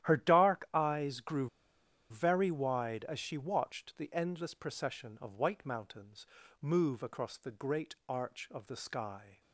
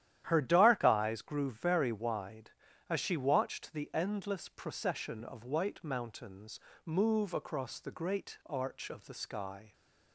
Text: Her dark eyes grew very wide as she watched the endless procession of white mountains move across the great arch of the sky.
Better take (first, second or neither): second